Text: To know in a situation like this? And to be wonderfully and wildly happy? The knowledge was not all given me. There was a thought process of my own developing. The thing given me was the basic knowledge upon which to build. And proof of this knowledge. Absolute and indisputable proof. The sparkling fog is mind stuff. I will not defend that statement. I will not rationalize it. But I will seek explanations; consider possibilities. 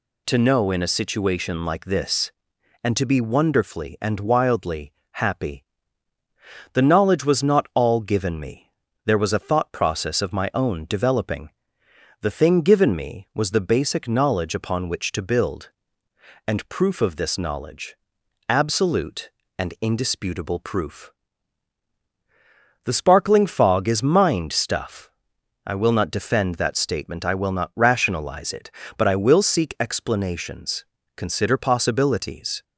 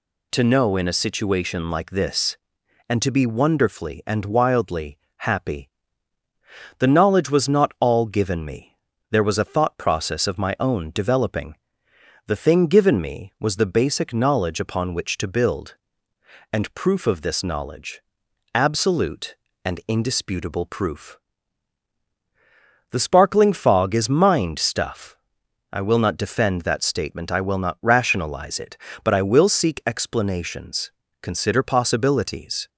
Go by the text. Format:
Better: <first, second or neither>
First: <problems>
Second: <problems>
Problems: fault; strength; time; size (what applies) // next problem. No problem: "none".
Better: neither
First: pauses between "wildly" and "happy"; slight; at 4.9 s; 0.20 s long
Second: pauses between "wildly" and "happy"; slight; at 4.9 s; 0.20 s long